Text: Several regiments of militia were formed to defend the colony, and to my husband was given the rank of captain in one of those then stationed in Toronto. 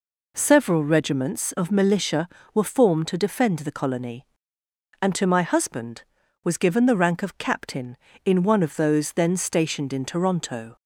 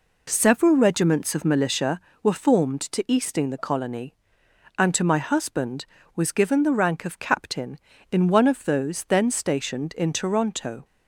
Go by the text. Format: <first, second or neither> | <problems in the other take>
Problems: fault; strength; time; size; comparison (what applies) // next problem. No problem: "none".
first | says "easting" for "defend"; at 3.0 s